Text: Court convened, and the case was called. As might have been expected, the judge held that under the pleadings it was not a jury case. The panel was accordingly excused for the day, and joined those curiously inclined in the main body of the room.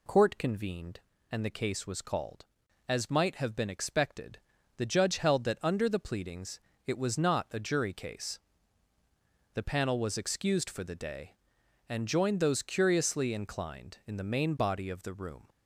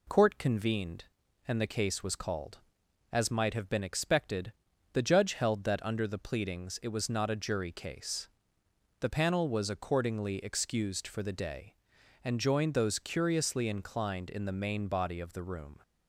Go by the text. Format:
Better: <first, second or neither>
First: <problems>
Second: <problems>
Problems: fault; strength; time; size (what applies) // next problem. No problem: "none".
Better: second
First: pauses between "pleadings" and "it"; slight; at 6.6 s; 0.24 s long // skips "accordingly"; at 10.1 s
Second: none